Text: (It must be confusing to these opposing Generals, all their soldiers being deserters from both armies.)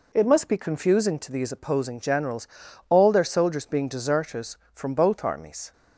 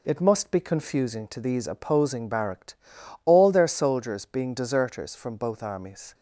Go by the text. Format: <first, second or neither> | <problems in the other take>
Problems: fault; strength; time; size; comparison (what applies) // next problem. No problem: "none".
first | says "Barracked" for "Generals"; at 2.2 s